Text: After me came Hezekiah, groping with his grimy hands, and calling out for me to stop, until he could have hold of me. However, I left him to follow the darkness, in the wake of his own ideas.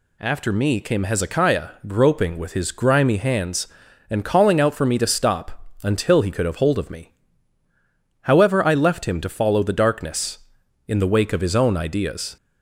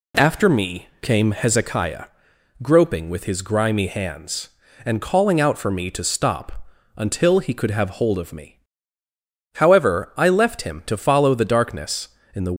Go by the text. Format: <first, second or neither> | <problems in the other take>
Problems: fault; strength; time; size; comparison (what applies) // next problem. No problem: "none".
first | stops before "wake of his own ideas"; at 12.5 s